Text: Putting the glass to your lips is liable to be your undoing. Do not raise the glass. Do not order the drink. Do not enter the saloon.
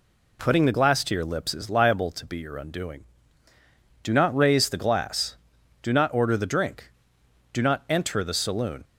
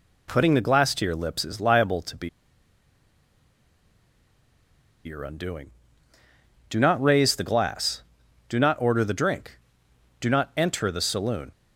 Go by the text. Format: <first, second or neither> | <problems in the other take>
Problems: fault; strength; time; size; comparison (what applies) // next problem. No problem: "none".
first | pauses between "be" and "your"; strong; at 2.2 s; 2.7 s long